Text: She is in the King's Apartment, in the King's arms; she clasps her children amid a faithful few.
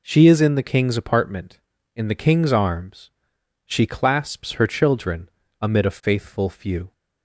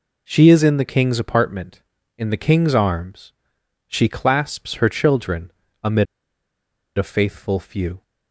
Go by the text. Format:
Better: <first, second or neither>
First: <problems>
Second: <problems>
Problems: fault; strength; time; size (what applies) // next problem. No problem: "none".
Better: first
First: pauses between "children" and "amid"; slight; at 5.2 s; 0.32 s long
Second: pauses between "children" and "amid"; slight; at 5.5 s; 0.32 s long // pauses between "amid" and "a"; noticeable; at 6.0 s; 0.92 s long